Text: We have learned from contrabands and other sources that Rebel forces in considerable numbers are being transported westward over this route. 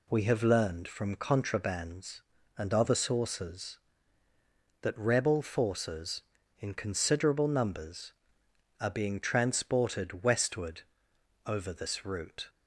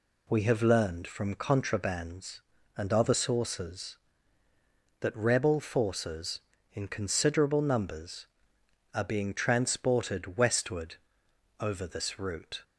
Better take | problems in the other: neither | pauses between "westward" and "over"; noticeable; the same in both

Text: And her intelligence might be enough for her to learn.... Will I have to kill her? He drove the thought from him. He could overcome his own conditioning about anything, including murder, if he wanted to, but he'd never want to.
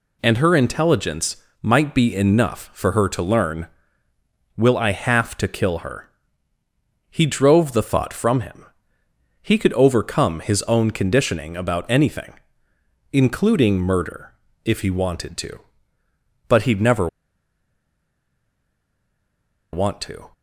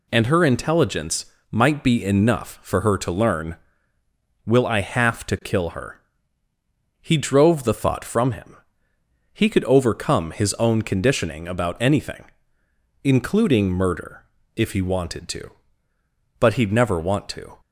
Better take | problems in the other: second | pauses between "intelligence" and "might"; slight; at 1.3 s; 0.24 s long; slight in the second // pauses between "never" and "want"; strong; at 17.0 s; 2.6 s long

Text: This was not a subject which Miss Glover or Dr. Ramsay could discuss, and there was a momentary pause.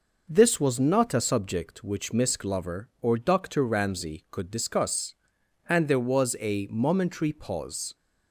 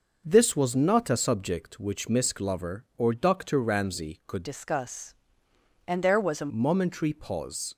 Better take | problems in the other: first | changes voice from "discuss" to "a"; from 4.4 to 6.5 s; 2.1 s long

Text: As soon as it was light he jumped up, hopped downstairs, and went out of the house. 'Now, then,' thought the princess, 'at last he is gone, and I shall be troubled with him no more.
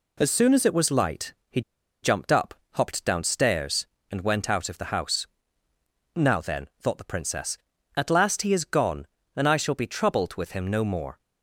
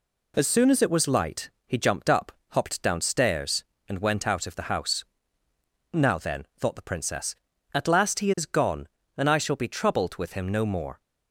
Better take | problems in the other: second | pauses between "light" and "he"; slight; at 1.3 s; 0.16 s long; slight in the second // pauses between "he" and "jumped"; at 1.6 s; 0.42 s long

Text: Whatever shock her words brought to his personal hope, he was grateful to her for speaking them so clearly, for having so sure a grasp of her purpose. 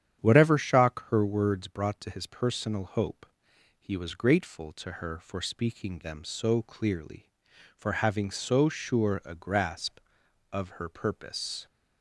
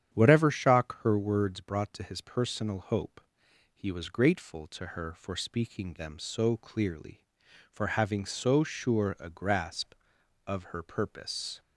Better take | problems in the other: neither | starts louder than the rest; strong; the same in both

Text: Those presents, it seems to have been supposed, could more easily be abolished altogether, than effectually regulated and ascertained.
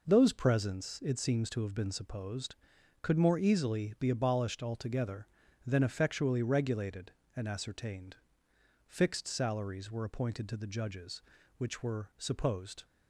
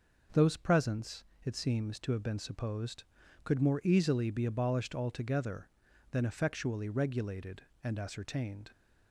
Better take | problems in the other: second | goes on to say "Fixed salaries were appointed to the judges which were supposed"; strong; from 8.8 s on; 3.9 s long

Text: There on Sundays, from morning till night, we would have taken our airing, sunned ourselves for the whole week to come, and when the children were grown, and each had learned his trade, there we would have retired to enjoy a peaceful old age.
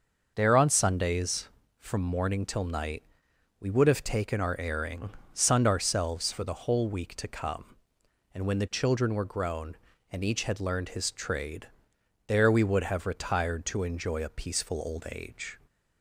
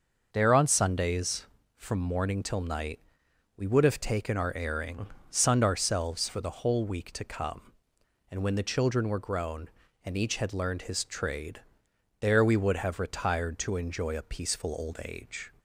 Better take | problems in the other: neither | starts louder than the rest; the same in both

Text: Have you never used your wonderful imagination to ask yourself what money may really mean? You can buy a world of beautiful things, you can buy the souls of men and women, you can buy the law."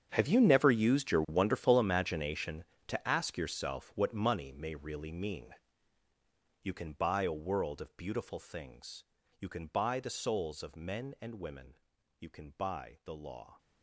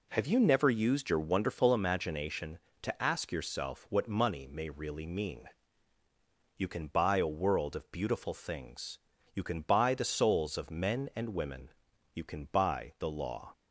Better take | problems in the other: second | gets quieter; strong; throughout; 16.5 dB

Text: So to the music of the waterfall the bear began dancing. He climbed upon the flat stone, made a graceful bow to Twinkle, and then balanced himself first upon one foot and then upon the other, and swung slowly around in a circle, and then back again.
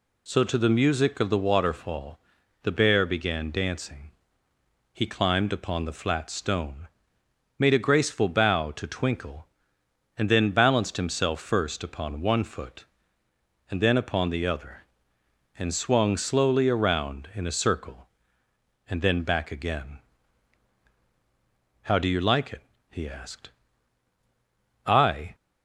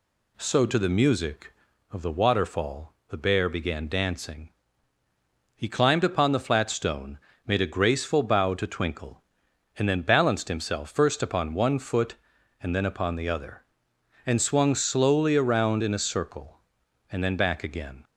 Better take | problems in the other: second | pauses between "waterfall" and "the"; at 2.1 s; 0.44 s long; slight in the second // goes on to say "How do you like it he asked I"; strong; from 21.8 s on; 3.5 s long

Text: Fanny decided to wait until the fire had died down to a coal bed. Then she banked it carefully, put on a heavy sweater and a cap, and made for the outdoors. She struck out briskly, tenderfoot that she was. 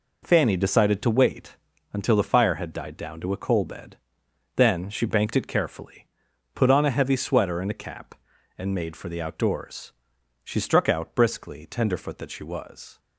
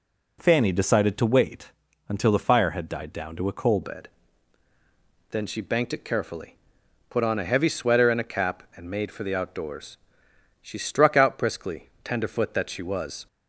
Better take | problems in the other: first | pauses between "wait" and "until"; slight; at 1.7 s; 0.36 s long; slight in the first // changes voice at "bed"; from 3.8 s on; 9.4 s long

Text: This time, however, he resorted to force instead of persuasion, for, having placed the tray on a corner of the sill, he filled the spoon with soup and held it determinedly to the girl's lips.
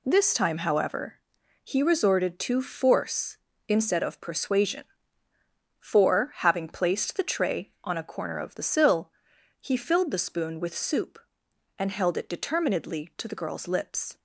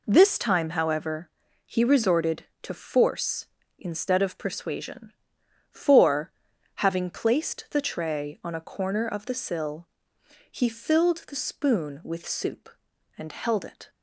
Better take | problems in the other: first | stops before "determinedly to the girl's lips"; at 13.8 s

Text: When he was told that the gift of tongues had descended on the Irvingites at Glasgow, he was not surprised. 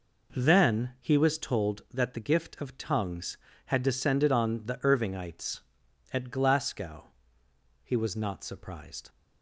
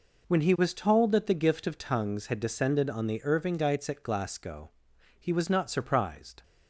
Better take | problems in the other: second | says "Then" for "When"; at 0.3 s

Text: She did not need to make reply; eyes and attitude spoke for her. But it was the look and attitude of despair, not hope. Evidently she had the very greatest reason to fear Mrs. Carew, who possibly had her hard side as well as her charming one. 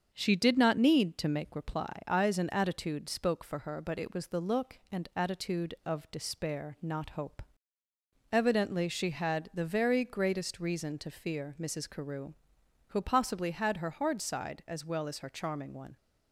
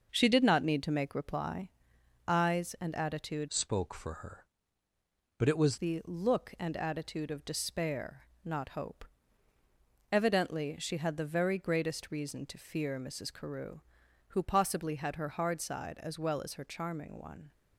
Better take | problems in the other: first | starts louder than the rest; noticeable; until 1.1 s; 6 dB; also in the first // changes voice from "spoke" to "was"; from 3.4 to 5.7 s; 2.3 s long

